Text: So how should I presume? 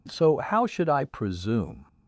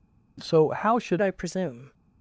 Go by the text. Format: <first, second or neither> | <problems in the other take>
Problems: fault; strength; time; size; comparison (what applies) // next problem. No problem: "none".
first | changes voice at "I"; from 1.2 s on; 0.7 s long